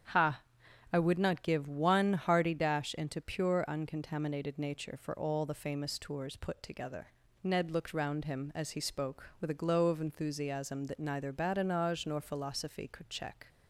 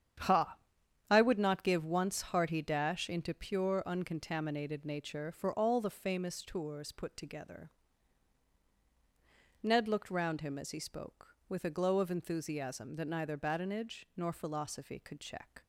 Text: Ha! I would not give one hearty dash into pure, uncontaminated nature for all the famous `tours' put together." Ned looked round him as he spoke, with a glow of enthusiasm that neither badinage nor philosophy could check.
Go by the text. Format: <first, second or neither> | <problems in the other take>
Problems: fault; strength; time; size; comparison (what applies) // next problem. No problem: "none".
first | starts louder than the rest; strong; until 1.7 s; 8.5 dB; strong in the first // says "once" for "one"; at 1.8 s